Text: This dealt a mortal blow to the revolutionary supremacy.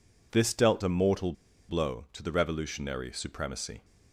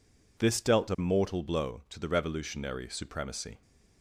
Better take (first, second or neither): second